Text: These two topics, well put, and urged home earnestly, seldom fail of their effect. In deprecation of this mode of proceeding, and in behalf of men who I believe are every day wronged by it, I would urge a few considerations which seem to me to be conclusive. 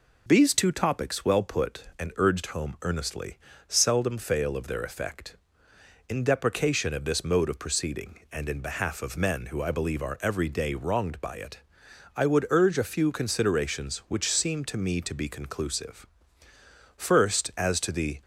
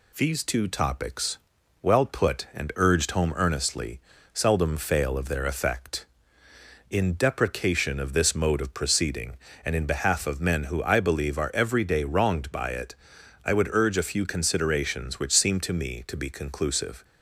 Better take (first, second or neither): second